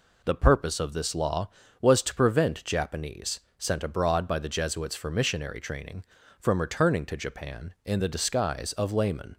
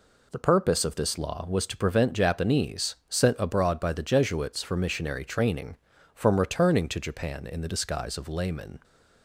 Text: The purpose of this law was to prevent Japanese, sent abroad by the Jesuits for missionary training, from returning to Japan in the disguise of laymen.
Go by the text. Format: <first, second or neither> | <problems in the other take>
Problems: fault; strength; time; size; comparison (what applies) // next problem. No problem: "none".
neither | none